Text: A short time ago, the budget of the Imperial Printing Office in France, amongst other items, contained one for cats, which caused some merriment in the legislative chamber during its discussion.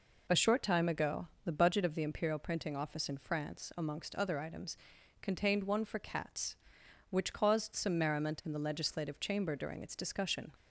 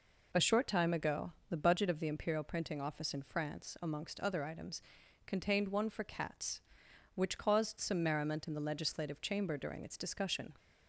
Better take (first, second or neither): neither